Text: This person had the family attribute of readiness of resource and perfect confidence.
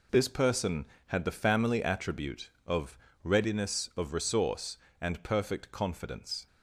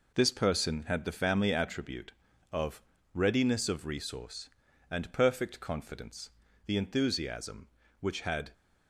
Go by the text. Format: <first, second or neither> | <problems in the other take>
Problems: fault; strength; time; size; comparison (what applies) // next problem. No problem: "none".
first | pauses between "of" and "readiness"; slight; at 2.8 s; 0.32 s long; slight in the first // goes on to say "The enthusiasm which had"; strong; from 6.6 s on; 1.8 s long